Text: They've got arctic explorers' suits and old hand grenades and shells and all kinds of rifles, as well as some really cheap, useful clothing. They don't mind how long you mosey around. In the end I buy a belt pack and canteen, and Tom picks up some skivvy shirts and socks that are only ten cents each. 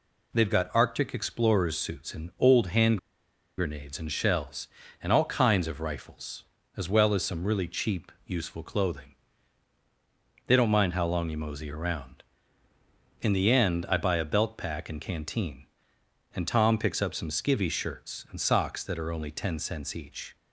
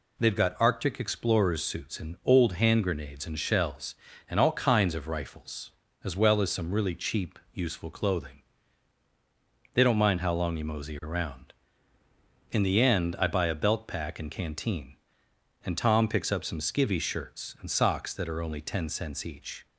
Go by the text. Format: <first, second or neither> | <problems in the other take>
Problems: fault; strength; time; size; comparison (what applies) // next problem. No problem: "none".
second | pauses between "hand" and "grenades"; noticeable; at 2.9 s; 0.61 s long